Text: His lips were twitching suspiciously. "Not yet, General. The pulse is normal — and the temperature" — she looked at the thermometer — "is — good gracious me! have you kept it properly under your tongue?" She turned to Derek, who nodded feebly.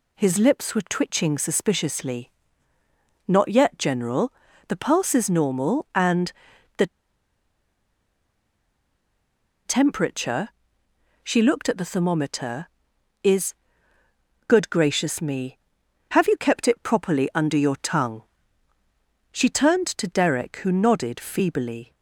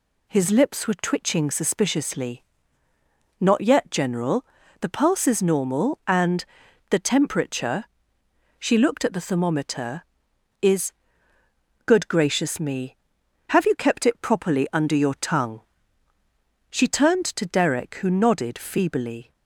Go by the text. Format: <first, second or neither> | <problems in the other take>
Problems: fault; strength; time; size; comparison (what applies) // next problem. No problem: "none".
second | pauses between "and" and "the"; noticeable; at 6.3 s; 0.46 s long; noticeable in the second // pauses between "the" and "temperature"; strong; at 6.8 s; 2.7 s long